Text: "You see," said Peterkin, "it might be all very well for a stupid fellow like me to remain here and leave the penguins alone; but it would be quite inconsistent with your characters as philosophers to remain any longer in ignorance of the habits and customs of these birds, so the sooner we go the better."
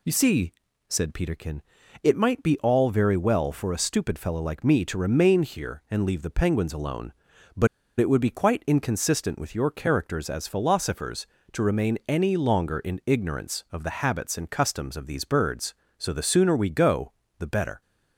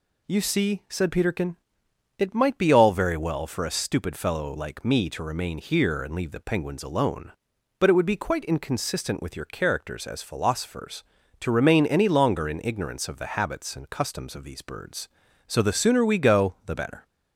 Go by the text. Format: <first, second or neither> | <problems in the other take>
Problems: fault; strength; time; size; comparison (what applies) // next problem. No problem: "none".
second | pauses between "but" and "it"; slight; at 7.6 s; 0.31 s long // pauses between "go" and "the"; slight; at 17.1 s; 0.28 s long